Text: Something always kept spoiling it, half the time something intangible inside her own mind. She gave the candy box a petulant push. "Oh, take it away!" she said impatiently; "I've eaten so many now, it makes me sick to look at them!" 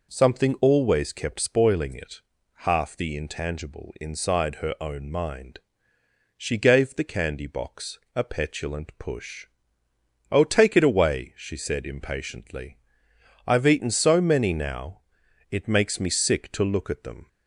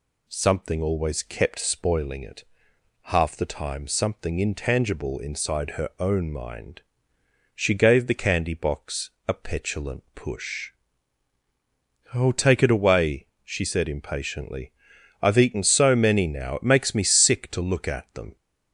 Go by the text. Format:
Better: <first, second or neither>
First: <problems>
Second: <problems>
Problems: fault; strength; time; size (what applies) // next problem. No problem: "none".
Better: second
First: skips "time something"; at 3.1 s // pauses between "box" and "a"; slight; at 7.9 s; 0.16 s long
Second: pauses between "box" and "a"; slight; at 9.0 s; 0.16 s long